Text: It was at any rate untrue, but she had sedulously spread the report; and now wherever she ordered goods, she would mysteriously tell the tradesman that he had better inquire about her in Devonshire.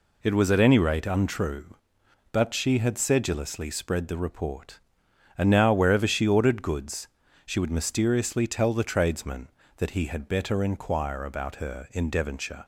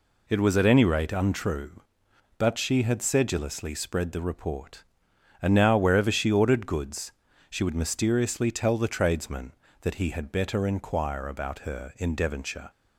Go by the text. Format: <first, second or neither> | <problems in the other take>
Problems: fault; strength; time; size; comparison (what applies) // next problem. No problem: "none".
neither | none